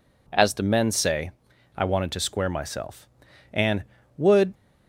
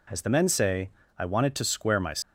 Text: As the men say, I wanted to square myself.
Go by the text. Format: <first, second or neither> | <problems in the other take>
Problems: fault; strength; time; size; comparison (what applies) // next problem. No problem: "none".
second | goes on to say "And would"; noticeable; from 3.5 s on; 1.0 s long